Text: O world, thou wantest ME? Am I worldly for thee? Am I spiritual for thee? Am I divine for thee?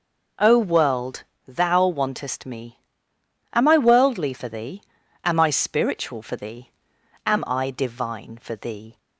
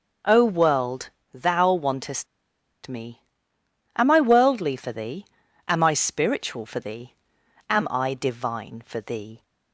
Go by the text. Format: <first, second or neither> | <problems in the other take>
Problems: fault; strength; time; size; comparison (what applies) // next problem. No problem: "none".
first | pauses between "wantest" and "ME"; noticeable; at 2.2 s; 0.59 s long